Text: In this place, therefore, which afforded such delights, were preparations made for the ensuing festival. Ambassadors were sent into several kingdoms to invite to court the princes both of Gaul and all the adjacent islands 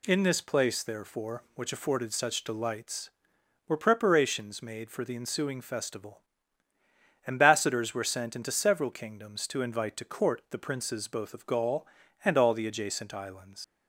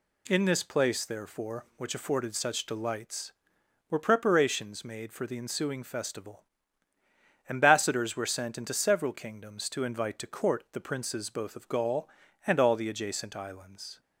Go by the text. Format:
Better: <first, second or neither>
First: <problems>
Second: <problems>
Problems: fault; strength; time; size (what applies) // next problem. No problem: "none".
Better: second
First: leaves "islands" unfinished; at 13.6 s; 140 ms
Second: none